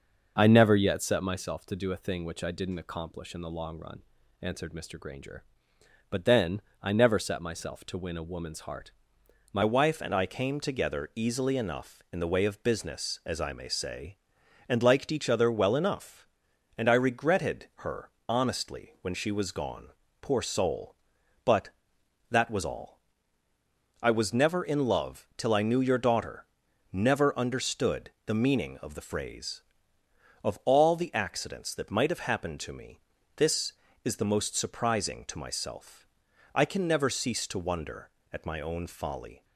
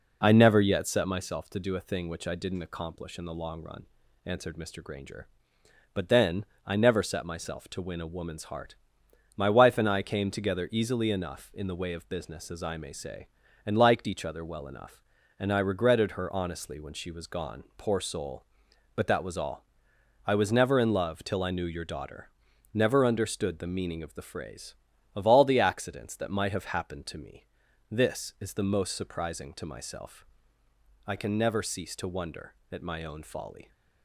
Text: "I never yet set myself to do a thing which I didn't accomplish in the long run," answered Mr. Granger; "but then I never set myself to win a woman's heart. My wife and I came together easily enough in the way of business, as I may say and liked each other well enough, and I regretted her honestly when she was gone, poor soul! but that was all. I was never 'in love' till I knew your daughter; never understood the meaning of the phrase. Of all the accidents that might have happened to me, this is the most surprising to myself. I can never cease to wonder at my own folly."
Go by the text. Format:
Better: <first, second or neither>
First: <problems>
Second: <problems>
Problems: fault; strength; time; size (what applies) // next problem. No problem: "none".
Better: second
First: pauses between "then" and "I"; slight; at 6.6 s; 0.22 s long // changes voice at "wife"; from 9.6 s on; 29.8 s long // pauses between "her" and "honestly"; slight; at 18.1 s; 0.18 s long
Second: pauses between "then" and "I"; slight; at 6.4 s; 0.22 s long